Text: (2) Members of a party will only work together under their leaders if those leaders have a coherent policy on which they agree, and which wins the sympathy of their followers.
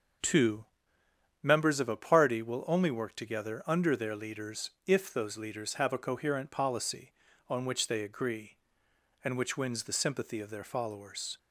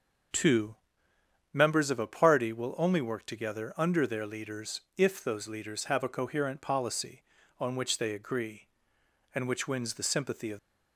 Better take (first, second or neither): first